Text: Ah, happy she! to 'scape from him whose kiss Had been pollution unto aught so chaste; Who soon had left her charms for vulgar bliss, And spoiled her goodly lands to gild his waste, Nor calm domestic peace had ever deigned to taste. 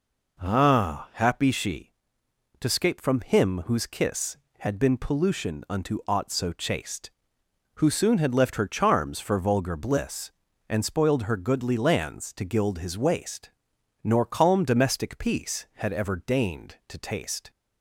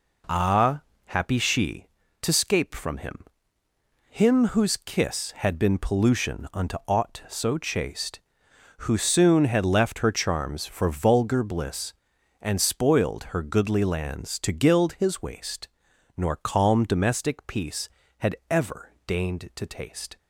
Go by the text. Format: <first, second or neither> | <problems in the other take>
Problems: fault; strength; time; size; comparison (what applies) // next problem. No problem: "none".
first | says "him" twice; at 4.0 s